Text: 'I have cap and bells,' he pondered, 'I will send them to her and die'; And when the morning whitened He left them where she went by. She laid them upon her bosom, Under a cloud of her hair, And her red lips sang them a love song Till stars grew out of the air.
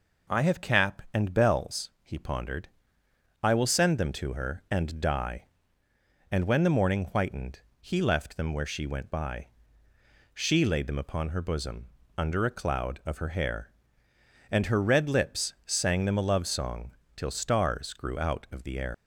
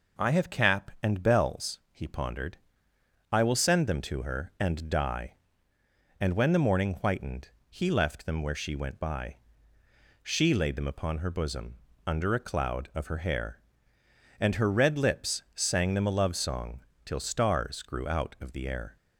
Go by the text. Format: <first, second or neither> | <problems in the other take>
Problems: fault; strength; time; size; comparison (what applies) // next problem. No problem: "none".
second | pauses between "whitened" and "He"; slight; at 7.6 s; 0.18 s long; slight in the second // pauses between "song" and "Till"; slight; at 16.9 s; 0.24 s long; slight in the second // leaves "air" unfinished; at 18.9 s; 125 ms